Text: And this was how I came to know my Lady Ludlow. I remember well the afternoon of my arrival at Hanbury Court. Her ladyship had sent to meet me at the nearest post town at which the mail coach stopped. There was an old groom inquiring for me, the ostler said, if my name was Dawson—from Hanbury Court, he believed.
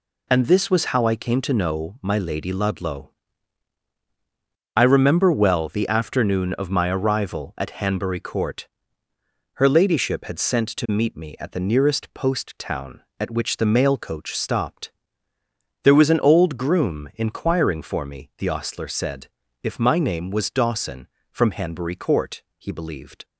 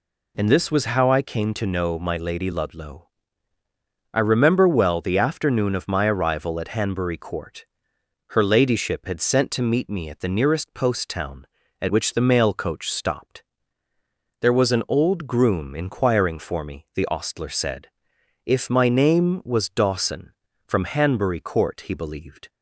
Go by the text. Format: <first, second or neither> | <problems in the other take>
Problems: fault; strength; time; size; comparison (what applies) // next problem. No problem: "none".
neither | none